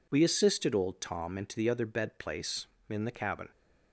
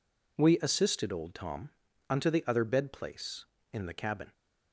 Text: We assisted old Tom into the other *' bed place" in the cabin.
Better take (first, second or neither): first